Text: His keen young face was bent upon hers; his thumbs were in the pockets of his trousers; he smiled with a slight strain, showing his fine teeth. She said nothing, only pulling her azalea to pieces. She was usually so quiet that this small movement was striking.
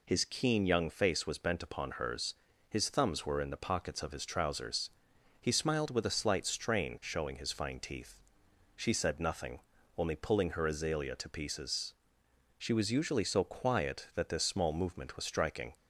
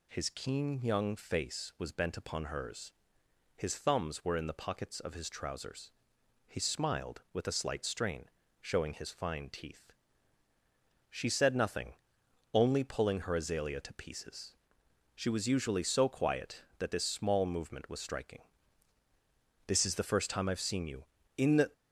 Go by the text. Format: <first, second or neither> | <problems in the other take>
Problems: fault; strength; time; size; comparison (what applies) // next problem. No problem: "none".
first | goes on to say "This is the first time I've seen you in the"; strong; from 19.6 s on; 2.0 s long